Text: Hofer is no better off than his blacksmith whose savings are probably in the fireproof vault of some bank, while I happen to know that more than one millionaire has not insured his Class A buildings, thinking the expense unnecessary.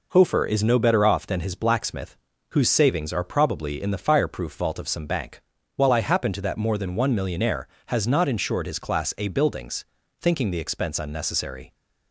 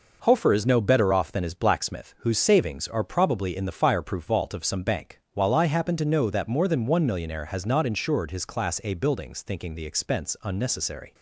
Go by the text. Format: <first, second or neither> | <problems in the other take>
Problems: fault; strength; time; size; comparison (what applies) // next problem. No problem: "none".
second | pauses between "blacksmith" and "whose"; slight; at 2.1 s; 0.36 s long // skips "know"; at 6.4 s